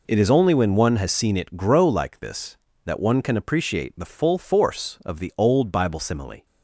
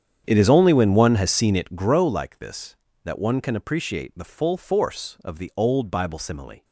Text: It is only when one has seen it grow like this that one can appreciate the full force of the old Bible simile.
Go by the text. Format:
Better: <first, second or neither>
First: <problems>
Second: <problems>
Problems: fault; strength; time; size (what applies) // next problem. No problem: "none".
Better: first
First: none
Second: starts louder than the rest; strong; until 2.0 s; 8.5 dB